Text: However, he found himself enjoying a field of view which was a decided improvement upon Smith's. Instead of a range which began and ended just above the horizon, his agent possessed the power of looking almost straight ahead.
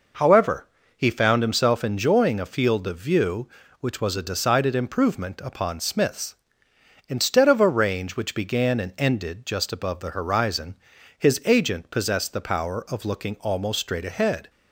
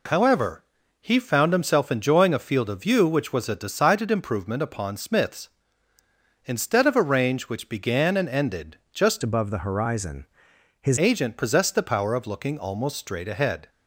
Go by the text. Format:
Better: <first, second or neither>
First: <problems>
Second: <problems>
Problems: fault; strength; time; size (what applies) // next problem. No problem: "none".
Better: first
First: none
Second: changes voice from "above" to "his"; from 9.2 to 10.9 s; 1.7 s long